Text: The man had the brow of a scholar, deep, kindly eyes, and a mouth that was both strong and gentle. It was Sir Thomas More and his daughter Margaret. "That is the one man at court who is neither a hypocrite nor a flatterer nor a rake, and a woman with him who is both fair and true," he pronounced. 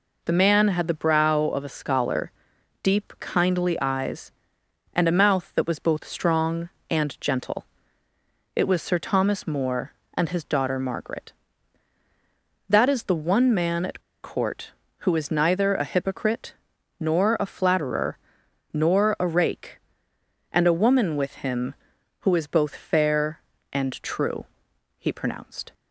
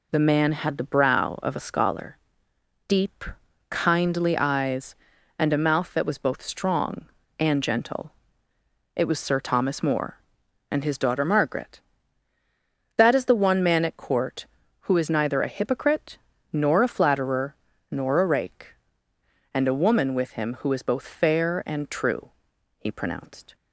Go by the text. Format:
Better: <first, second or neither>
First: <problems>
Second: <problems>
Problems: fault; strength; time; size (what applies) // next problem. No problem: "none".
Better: second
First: pauses between "at" and "court"; slight; at 13.9 s; 0.23 s long // pauses between "hypocrite" and "nor"; at 16.5 s; 0.44 s long // pauses between "flatterer" and "nor"; noticeable; at 18.1 s; 0.56 s long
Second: pauses between "hypocrite" and "nor"; slight; at 16.1 s; 0.34 s long // pauses between "flatterer" and "nor"; slight; at 17.5 s; 0.34 s long